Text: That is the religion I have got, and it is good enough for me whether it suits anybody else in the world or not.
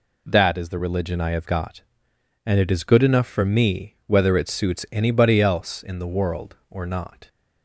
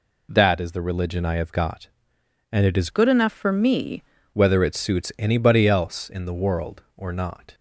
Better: first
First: none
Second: changes voice from "good" to "me"; from 2.8 to 4.0 s; 1.2 s long

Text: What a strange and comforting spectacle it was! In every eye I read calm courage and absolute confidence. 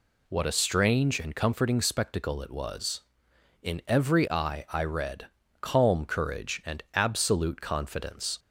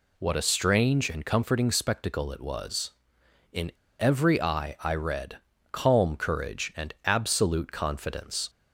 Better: first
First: pauses between "read" and "calm"; slight; at 5.2 s; 0.34 s long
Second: pauses between "In" and "every"; slight; at 3.6 s; 0.29 s long // pauses between "read" and "calm"; slight; at 5.3 s; 0.34 s long

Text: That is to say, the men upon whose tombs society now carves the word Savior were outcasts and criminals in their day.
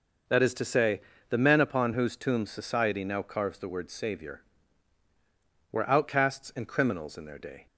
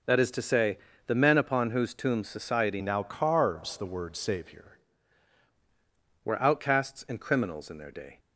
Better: first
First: none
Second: changes voice from "now" to "Savior"; from 2.8 to 4.7 s; 1.9 s long

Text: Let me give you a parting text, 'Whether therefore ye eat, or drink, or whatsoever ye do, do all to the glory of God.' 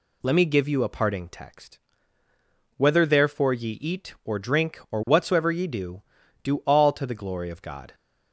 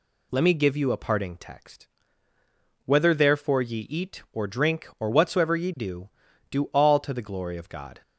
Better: neither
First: none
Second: none

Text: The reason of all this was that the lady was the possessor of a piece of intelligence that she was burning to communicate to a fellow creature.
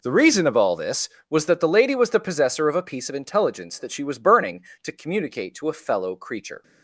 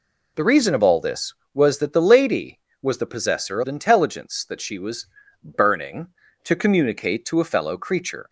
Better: first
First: none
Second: skips "of a piece"; at 3.6 s // pauses between "was" and "burning"; slight; at 5.0 s; 0.36 s long

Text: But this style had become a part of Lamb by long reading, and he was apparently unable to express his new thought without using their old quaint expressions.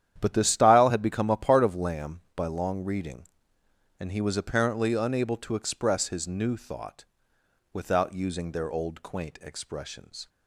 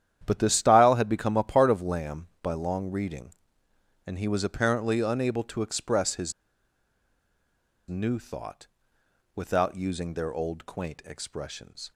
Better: first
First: starts louder than the rest; strong; until 1.2 s; 10 dB // pauses between "thought" and "without"; noticeable; at 7.0 s; 0.70 s long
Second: starts louder than the rest; strong; until 1.2 s; 10 dB // pauses between "his" and "new"; strong; at 6.3 s; 1.5 s long // pauses between "thought" and "without"; noticeable; at 8.6 s; 0.70 s long

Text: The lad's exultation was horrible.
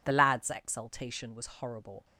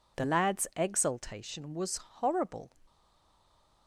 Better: first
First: none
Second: stays silent after the last word; from 2.8 s on; 1.0 s long

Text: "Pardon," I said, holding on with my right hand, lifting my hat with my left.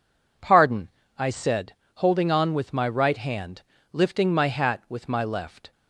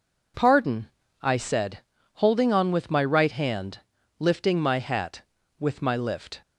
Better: first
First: none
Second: says "lift" for "left"; at 5.9 s

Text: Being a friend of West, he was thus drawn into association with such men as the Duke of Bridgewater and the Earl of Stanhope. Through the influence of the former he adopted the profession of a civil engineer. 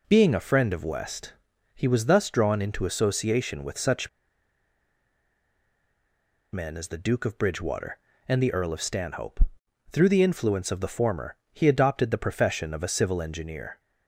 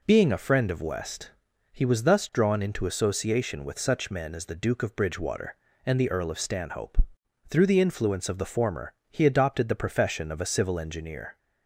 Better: second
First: pauses between "such" and "men"; strong; at 4.0 s; 2.4 s long // pauses between "former" and "he"; slight; at 11.3 s; 0.16 s long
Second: pauses between "former" and "he"; slight; at 8.9 s; 0.16 s long

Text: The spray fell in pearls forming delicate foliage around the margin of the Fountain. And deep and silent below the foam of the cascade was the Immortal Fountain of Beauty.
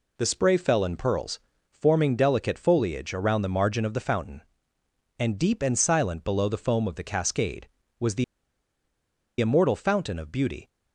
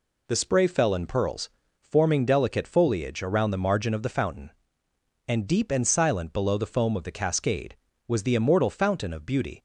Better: second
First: pauses between "pearls" and "forming"; slight; at 1.3 s; 0.32 s long // pauses between "the" and "Immortal"; at 8.2 s; 1.1 s long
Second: pauses between "pearls" and "forming"; slight; at 1.4 s; 0.32 s long

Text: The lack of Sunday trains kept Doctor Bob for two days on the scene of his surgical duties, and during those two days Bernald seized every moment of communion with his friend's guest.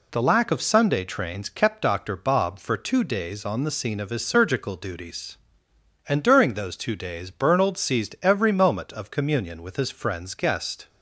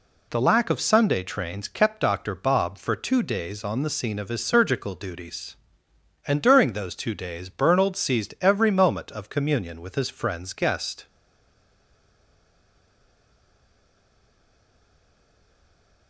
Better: first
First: none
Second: stays silent after the last word; strong; from 11.0 s on; 5.0 s long

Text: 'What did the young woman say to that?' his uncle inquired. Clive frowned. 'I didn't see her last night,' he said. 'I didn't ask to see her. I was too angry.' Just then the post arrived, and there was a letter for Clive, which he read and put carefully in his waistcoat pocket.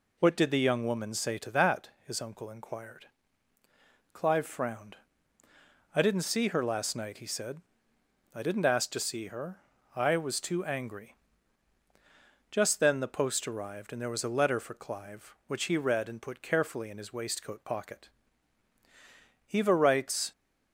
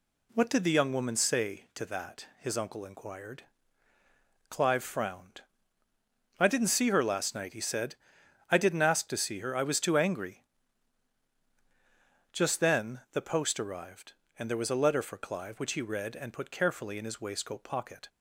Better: second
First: goes on to say "Eva writes"; noticeable; from 19.5 s on; 0.78 s long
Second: none

